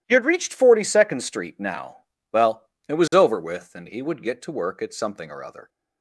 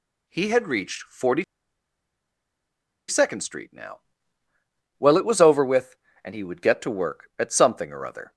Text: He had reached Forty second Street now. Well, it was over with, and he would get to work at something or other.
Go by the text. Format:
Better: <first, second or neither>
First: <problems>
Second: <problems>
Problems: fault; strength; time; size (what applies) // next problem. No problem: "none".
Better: first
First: none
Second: pauses between "Forty" and "second"; strong; at 1.4 s; 1.6 s long